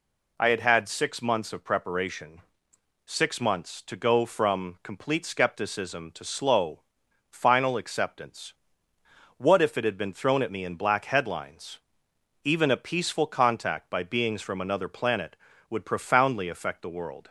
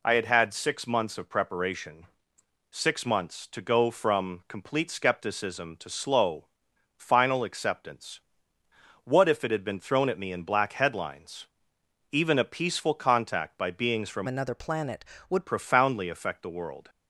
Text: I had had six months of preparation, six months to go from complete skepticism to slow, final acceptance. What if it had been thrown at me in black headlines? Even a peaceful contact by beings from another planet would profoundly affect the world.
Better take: first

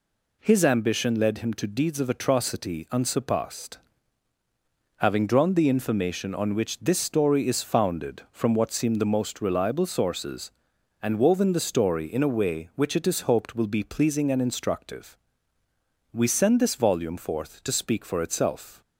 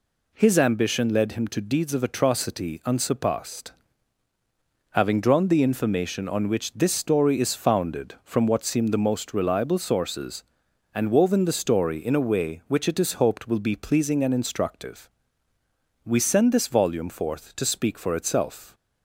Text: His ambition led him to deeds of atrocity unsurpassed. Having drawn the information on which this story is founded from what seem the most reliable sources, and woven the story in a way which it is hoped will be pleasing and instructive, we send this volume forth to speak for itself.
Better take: neither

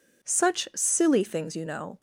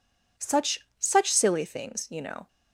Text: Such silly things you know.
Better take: first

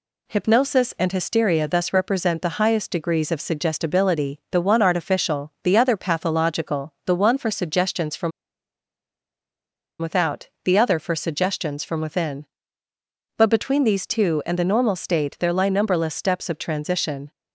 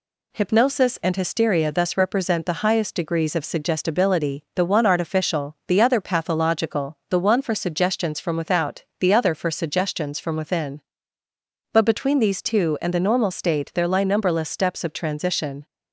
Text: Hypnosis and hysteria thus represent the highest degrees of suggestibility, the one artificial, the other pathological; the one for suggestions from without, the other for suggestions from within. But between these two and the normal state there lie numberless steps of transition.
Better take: second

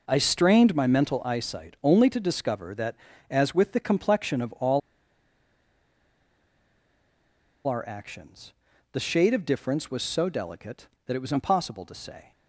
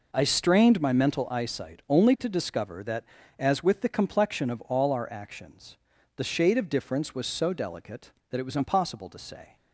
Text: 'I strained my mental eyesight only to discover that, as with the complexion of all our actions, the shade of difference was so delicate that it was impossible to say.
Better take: second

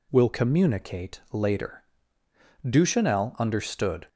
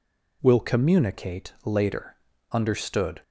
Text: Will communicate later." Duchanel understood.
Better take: first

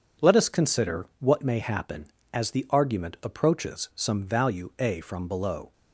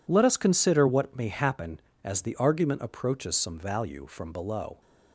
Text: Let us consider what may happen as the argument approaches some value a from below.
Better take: first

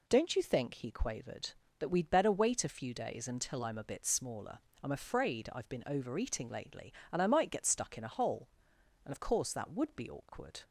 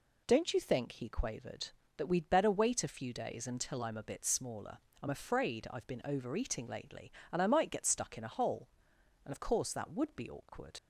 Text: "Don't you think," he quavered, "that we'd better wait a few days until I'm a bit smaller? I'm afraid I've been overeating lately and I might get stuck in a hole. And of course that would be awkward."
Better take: first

